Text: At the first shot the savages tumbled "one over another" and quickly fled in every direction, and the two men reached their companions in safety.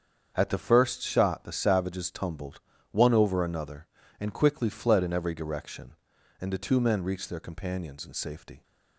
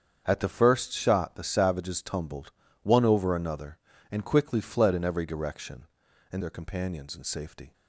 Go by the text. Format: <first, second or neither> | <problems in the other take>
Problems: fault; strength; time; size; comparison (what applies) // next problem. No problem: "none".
first | starts louder than the rest; strong; until 1.2 s; 7.5 dB; strong in the first // pauses between "tumbled" and "one"; slight; at 2.4 s; 0.32 s long; slight in the first // skips "the two men reached"; at 6.4 s